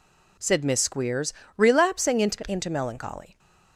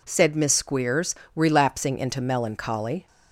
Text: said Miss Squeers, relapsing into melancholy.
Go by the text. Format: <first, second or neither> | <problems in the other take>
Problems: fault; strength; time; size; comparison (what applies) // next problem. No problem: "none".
second | says "into" twice; at 2.4 s